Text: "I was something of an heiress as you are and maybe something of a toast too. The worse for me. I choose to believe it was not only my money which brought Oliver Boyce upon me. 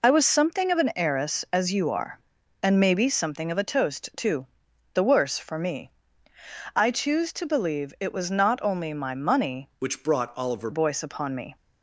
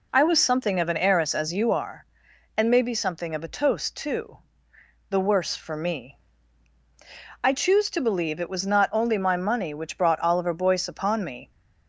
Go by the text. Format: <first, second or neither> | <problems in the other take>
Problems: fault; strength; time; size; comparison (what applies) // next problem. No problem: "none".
second | changes voice from "which" to "Oliver"; from 9.7 to 10.6 s; 0.9 s long